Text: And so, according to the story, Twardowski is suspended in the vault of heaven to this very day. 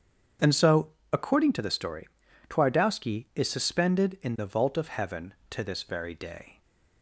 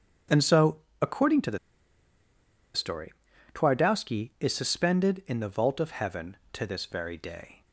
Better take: first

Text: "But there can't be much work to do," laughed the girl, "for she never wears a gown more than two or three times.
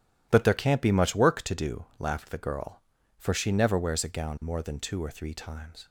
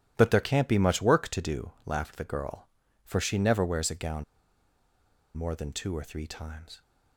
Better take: first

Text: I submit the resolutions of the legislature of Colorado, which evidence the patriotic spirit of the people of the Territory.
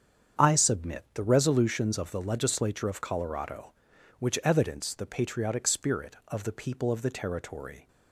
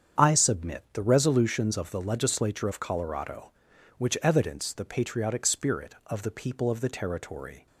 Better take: neither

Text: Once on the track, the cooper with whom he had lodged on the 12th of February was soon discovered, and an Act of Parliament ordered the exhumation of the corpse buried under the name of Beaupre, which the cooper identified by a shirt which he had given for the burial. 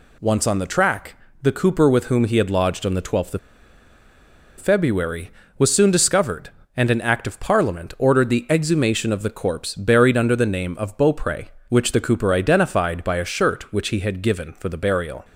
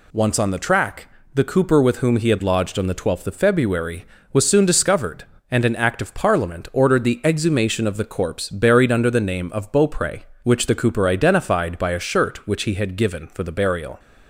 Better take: second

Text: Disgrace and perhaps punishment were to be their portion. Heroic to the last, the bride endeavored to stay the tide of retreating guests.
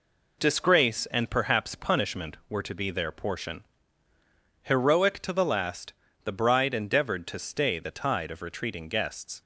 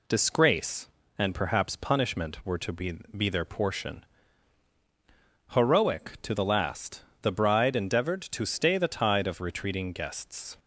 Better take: first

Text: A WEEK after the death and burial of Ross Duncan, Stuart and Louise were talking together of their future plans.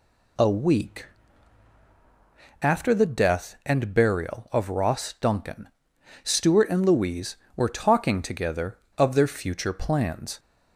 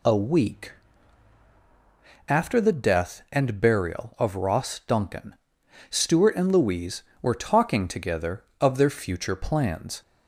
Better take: neither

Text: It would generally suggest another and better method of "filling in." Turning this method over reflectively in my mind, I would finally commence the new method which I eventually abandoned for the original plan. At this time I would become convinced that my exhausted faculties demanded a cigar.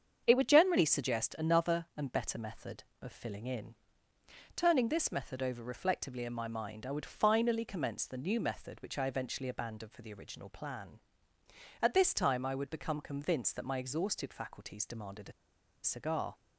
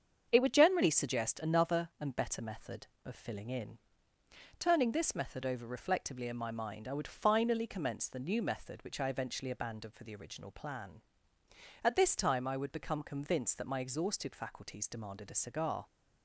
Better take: second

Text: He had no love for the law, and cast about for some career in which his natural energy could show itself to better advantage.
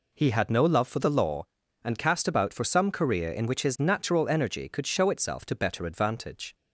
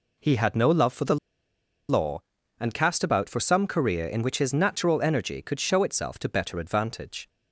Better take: first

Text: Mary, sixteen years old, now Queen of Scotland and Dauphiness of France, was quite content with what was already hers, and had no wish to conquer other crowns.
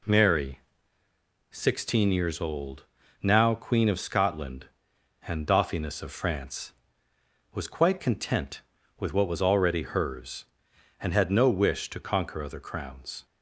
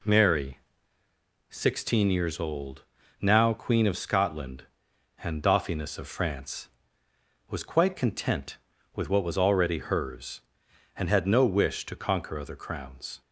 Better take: neither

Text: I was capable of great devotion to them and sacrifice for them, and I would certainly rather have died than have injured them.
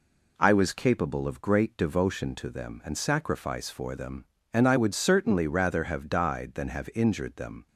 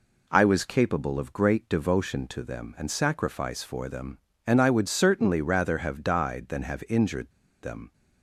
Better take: first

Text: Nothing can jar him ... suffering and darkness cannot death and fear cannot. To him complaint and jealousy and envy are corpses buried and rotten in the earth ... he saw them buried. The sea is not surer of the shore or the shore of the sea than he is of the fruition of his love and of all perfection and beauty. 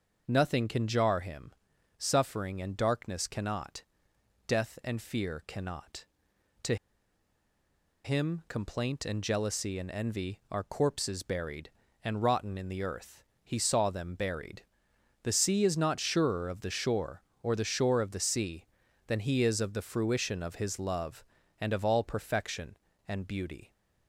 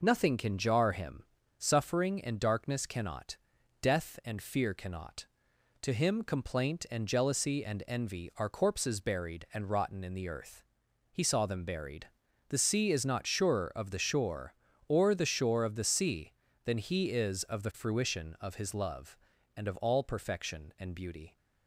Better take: second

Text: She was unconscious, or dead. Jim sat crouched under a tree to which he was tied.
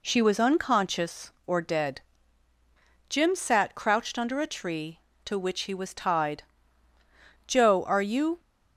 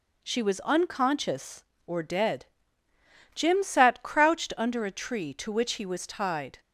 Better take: second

